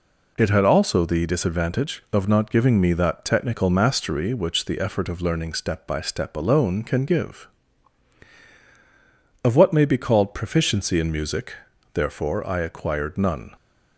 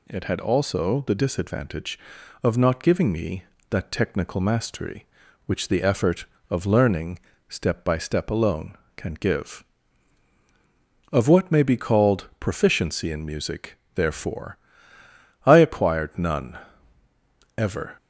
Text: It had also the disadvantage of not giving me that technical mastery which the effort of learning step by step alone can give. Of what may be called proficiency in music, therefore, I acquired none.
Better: first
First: none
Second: pauses between "learning" and "step"; slight; at 7.1 s; 0.30 s long // goes on to say "Ever"; slight; from 17.5 s on; 0.40 s long

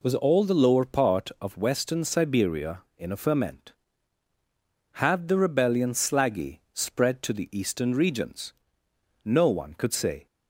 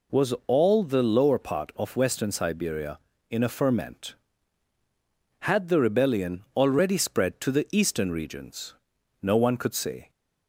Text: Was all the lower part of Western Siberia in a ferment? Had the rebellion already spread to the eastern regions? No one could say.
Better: second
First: says "slaggy" for "already"; at 5.9 s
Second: none

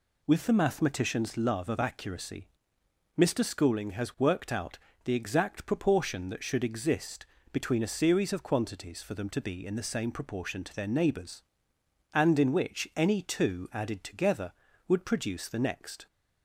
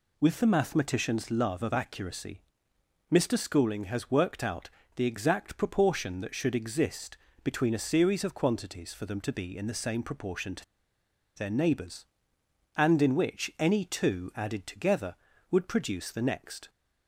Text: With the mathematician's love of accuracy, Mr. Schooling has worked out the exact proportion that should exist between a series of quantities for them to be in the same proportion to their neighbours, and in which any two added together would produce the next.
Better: first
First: pauses between "out" and "the"; slight; at 4.7 s; 0.26 s long // pauses between "exist" and "between"; slight; at 7.2 s; 0.26 s long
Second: pauses between "out" and "the"; slight; at 4.6 s; 0.26 s long // pauses between "exist" and "between"; slight; at 7.1 s; 0.26 s long // pauses between "to" and "their"; noticeable; at 10.6 s; 0.72 s long

